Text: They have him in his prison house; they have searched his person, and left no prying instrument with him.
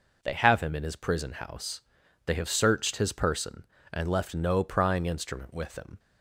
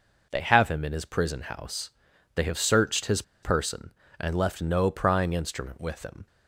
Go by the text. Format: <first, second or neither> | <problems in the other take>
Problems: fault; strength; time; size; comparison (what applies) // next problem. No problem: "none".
first | pauses between "his" and "person"; slight; at 3.2 s; 0.20 s long